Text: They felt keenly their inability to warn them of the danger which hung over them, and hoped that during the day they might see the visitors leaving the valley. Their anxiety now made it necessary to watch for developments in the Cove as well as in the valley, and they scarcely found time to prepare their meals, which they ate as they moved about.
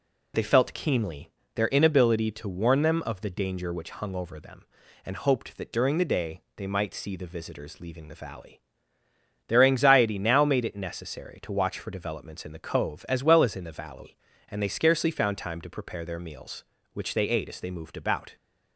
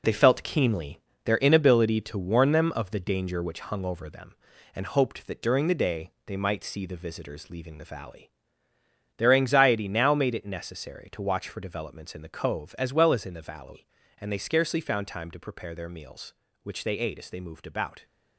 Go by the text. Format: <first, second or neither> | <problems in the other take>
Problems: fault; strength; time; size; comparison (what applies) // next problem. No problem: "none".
first | gets quieter; strong; throughout; 8.5 dB // pauses between "keenly" and "their"; slight; at 0.9 s; 0.26 s long; slight in the first // pauses between "day" and "they"; slight; at 6.1 s; 0.16 s long; slight in the first